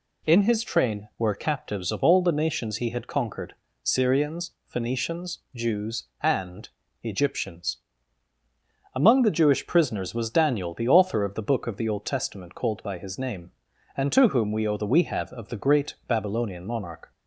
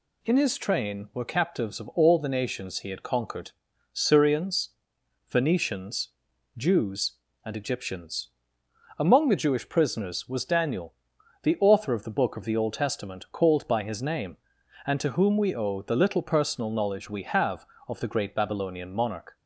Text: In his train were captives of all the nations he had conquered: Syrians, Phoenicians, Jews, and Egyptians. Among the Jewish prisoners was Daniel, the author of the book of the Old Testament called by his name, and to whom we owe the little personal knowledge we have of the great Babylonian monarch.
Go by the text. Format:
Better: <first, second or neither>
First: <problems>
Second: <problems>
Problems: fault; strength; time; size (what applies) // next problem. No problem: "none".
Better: second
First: pauses between "and" and "Egyptians"; slight; at 6.6 s; 0.32 s long // skips "little personal knowledge"; at 14.8 s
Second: none